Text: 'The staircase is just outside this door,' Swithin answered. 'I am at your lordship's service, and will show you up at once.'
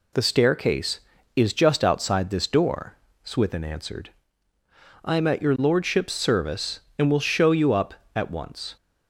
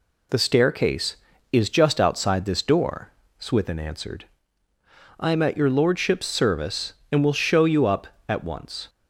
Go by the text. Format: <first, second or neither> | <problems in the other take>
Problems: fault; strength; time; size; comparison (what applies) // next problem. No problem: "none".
neither | none